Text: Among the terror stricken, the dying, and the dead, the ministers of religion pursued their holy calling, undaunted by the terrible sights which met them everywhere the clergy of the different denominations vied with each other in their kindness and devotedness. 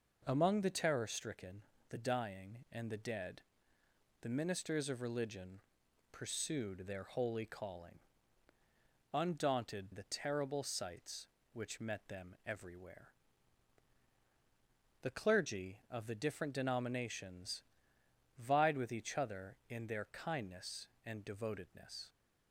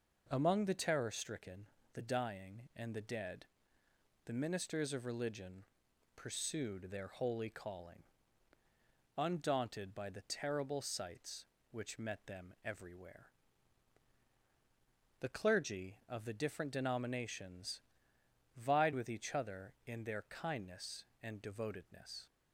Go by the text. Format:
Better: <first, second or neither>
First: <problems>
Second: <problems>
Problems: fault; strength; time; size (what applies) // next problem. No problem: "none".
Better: second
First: pauses between "religion" and "pursued"; noticeable; at 5.5 s; 0.54 s long // skips "by"; at 9.9 s // pauses between "everywhere" and "the"; strong; at 13.0 s; 1.9 s long // pauses between "denominations" and "vied"; noticeable; at 17.6 s; 0.74 s long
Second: pauses between "religion" and "pursued"; noticeable; at 5.6 s; 0.54 s long // pauses between "everywhere" and "the"; strong; at 13.2 s; 1.9 s long // pauses between "denominations" and "vied"; noticeable; at 17.8 s; 0.74 s long